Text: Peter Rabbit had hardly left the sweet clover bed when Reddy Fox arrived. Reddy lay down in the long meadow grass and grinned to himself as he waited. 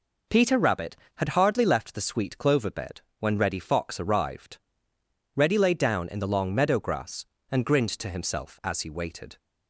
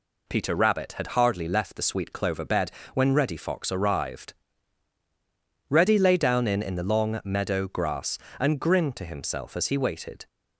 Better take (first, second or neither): first